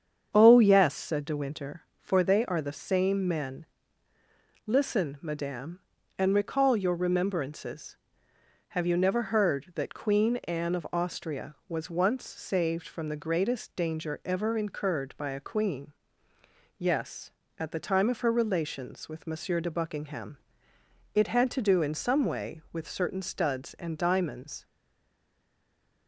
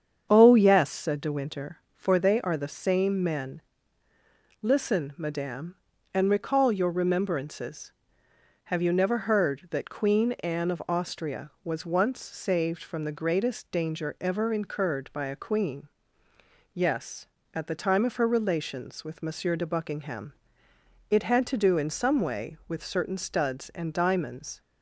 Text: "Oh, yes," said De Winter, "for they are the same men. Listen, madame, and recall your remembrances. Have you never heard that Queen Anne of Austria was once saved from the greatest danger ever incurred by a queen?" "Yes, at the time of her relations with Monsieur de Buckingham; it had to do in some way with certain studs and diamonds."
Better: second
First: starts louder than the rest; strong; until 1.3 s; 7.5 dB // stays silent after the last word; noticeable; from 24.6 s on; 1.4 s long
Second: starts louder than the rest; strong; until 1.3 s; 7.5 dB

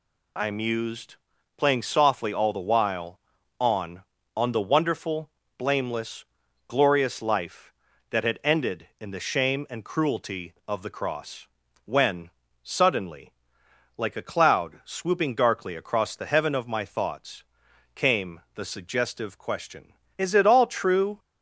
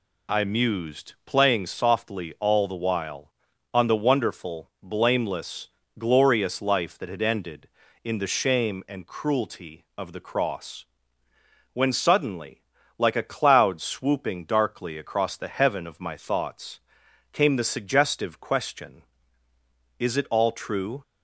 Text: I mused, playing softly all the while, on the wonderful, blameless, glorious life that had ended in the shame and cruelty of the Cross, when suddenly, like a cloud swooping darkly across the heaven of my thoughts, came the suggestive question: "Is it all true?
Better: second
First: says "on" twice; at 4.3 s // pauses between "when" and "suddenly"; slight; at 12.2 s; 0.34 s long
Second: none

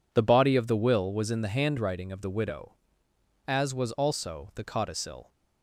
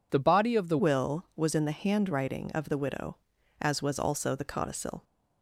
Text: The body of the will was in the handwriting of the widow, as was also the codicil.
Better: first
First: none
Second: changes voice at "will"; from 0.7 s on; 4.3 s long

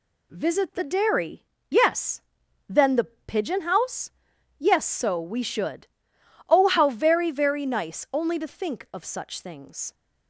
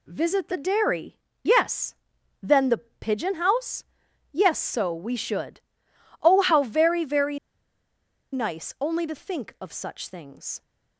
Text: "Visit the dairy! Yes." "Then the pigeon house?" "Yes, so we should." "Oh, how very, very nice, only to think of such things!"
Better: first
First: none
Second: pauses between "very" and "nice"; noticeable; at 7.3 s; 0.95 s long

